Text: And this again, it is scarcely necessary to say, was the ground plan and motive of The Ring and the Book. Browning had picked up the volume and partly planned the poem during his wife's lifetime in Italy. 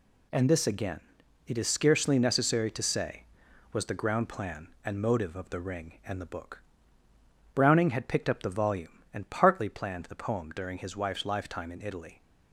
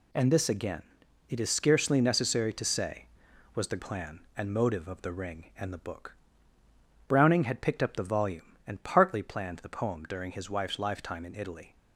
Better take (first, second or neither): first